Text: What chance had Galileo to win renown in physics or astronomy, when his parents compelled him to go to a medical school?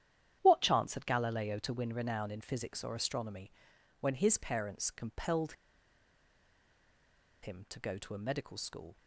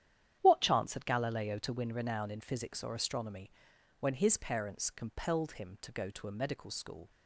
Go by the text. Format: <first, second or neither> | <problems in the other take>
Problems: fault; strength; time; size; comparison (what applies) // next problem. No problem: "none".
second | starts louder than the rest; strong; until 1.4 s; 10.5 dB; strong in the second // pauses between "compelled" and "him"; strong; at 5.5 s; 1.8 s long